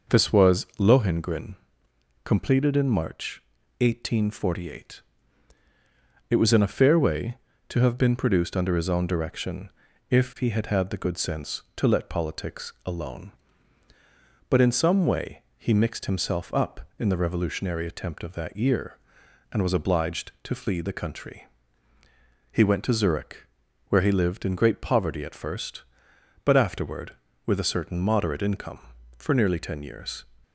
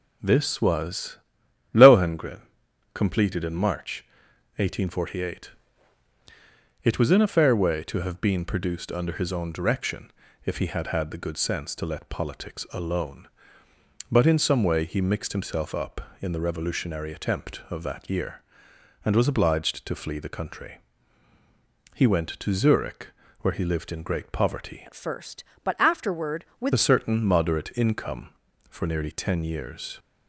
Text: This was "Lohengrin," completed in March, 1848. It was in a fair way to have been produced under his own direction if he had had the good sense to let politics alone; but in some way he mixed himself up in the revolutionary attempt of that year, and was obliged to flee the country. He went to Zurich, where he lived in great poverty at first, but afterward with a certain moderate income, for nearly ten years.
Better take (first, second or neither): first